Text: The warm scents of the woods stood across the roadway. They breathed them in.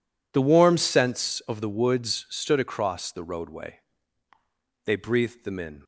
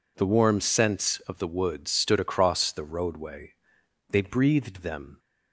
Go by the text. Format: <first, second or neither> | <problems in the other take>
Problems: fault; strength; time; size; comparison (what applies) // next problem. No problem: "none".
first | stops before "in"; at 5.1 s